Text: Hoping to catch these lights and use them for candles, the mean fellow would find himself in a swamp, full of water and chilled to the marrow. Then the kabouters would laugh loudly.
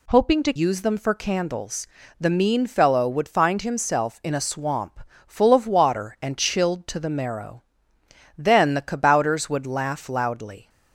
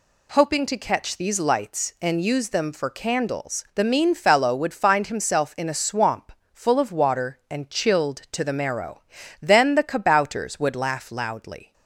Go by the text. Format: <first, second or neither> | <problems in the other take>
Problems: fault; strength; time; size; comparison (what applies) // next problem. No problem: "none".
second | skips "catch these lights and"; at 0.5 s